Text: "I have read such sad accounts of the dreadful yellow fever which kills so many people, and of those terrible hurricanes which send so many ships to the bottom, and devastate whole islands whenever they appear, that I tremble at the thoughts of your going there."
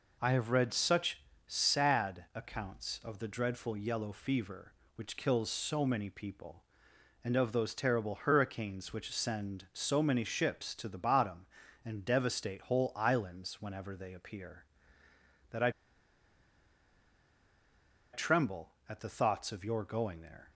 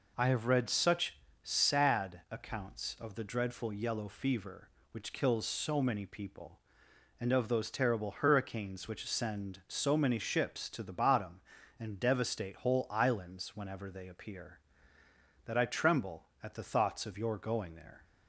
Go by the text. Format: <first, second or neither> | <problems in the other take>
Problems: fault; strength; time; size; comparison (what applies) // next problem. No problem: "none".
second | pauses between "such" and "sad"; slight; at 1.1 s; 0.26 s long; slight in the second // pauses between "I" and "tremble"; strong; at 15.6 s; 2.4 s long